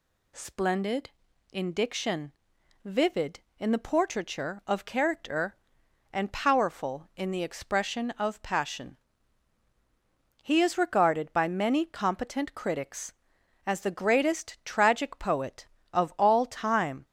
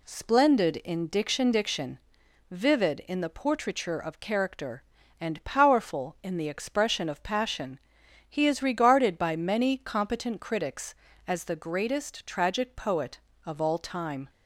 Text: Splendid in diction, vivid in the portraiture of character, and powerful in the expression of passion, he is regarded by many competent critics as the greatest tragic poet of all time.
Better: first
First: none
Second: says "diction" twice; at 1.5 s

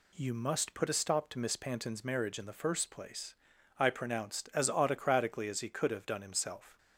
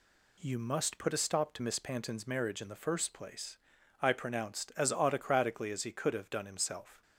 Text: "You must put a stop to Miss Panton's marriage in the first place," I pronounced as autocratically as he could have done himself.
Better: neither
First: none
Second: none

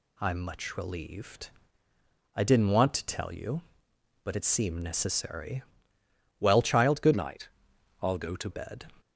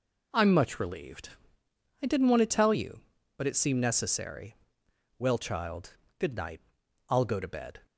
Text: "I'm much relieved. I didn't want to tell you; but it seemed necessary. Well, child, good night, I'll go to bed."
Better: second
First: changes voice from "night" to "to"; from 7.1 to 8.4 s; 1.3 s long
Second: none

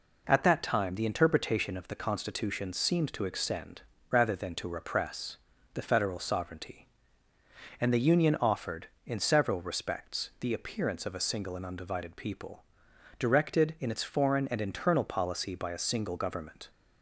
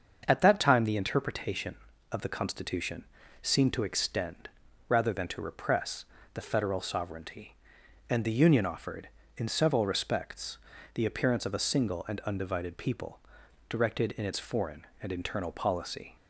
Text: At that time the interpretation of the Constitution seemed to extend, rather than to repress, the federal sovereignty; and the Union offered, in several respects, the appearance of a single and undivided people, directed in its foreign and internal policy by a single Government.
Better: first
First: none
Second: starts louder than the rest; until 1.2 s; 7 dB // pauses between "Constitution" and "seemed"; at 3.0 s; 0.38 s long // stops before "by a single Government"; at 16.1 s

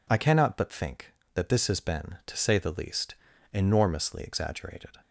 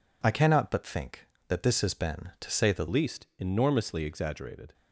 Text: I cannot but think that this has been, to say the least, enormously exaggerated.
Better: first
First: none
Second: changes voice at "least"; from 2.8 s on; 1.9 s long

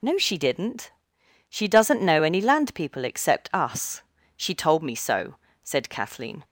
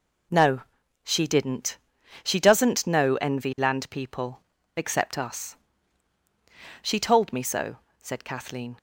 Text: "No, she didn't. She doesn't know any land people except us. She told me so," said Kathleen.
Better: first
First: none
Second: says "envy" for "any"; at 3.1 s // pauses between "people" and "except"; slight; at 4.4 s; 0.34 s long

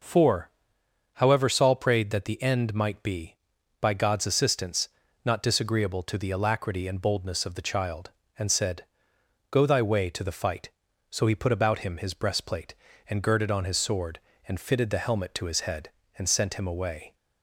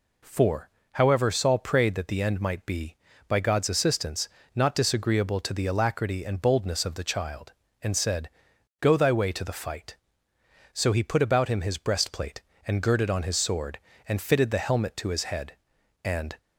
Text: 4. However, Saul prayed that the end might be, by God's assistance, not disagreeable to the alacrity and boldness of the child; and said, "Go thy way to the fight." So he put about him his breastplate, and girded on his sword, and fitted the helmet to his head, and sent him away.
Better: first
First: none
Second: stops before "sent him away"; at 16.3 s

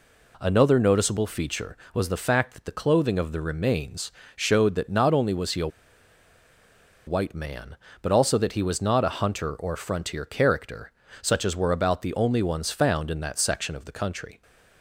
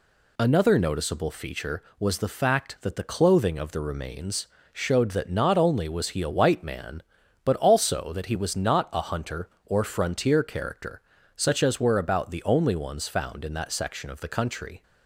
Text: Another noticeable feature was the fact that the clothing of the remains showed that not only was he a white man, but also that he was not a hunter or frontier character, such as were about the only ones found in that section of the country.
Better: second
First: pauses between "remains" and "showed"; slight; at 4.1 s; 0.24 s long // pauses between "a" and "white"; strong; at 5.6 s; 1.3 s long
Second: pauses between "remains" and "showed"; slight; at 4.4 s; 0.26 s long

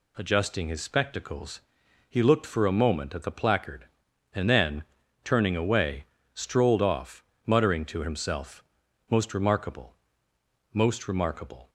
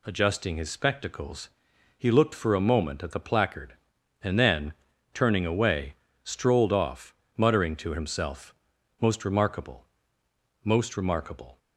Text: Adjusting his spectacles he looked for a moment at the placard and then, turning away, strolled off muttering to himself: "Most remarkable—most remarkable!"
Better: neither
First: pauses between "spectacles" and "he"; noticeable; at 1.6 s; 0.48 s long // pauses between "off" and "muttering"; slight; at 7.2 s; 0.22 s long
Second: pauses between "spectacles" and "he"; noticeable; at 1.5 s; 0.48 s long // pauses between "off" and "muttering"; slight; at 7.1 s; 0.22 s long

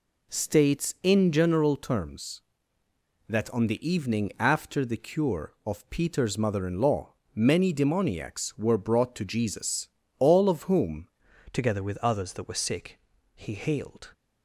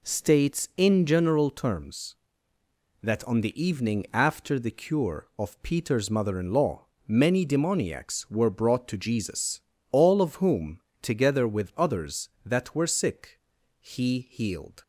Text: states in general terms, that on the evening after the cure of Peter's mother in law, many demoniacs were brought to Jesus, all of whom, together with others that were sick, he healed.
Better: second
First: changes voice at "together"; from 11.5 s on; 2.6 s long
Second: none

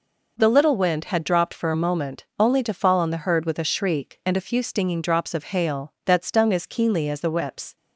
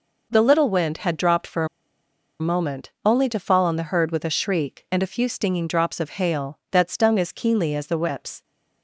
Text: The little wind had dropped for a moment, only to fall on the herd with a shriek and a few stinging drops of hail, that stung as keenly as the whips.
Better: first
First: none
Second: pauses between "a" and "moment"; noticeable; at 1.6 s; 0.75 s long

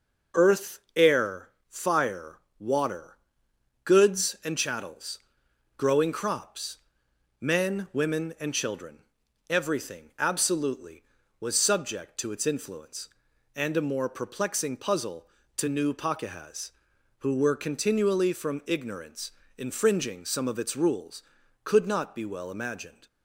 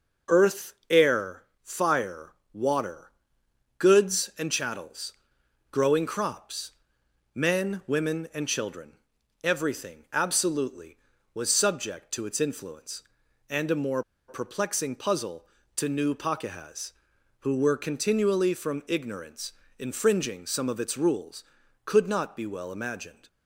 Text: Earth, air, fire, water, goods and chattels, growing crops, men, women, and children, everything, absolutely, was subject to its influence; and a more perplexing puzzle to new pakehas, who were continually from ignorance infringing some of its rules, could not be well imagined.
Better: first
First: pauses between "ignorance" and "infringing"; slight; at 19.3 s; 0.26 s long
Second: pauses between "more" and "perplexing"; slight; at 14.0 s; 0.27 s long // pauses between "ignorance" and "infringing"; slight; at 19.5 s; 0.26 s long

